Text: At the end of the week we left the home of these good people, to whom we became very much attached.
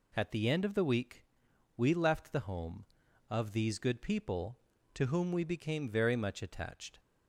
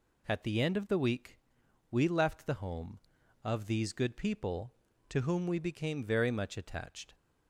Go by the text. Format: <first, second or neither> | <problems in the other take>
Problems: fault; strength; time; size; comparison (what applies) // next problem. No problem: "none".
neither | pauses between "week" and "we"; noticeable; the same in both